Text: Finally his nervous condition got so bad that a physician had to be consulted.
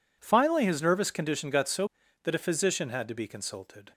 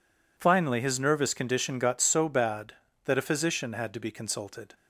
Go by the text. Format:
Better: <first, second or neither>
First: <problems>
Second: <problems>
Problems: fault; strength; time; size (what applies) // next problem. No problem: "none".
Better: second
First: skips "bad"; at 2.0 s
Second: none